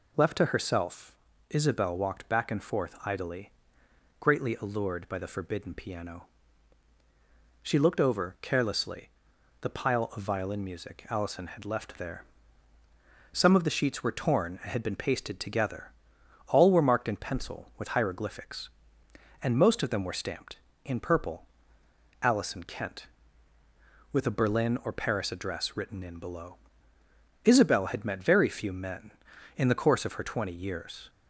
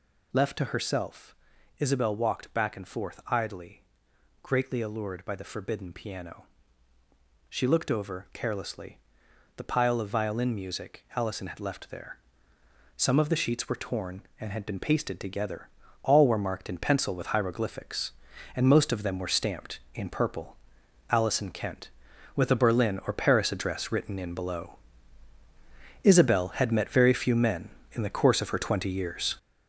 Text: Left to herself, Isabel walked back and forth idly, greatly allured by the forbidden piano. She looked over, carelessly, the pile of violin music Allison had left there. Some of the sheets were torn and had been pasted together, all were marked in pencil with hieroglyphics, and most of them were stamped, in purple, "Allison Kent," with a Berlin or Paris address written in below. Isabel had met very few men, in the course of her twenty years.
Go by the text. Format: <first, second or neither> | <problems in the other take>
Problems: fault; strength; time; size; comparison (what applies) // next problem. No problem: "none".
first | gets louder; strong; throughout; 8 dB